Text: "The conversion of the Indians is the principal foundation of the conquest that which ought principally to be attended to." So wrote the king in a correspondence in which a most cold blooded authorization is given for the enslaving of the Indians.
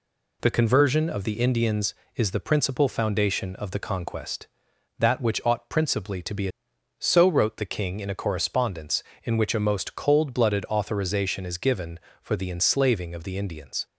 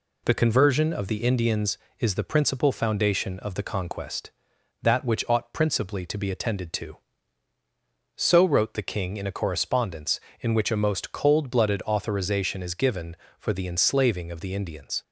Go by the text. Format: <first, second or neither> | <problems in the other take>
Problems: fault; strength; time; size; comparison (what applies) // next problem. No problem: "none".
second | skips "attended to"; at 6.7 s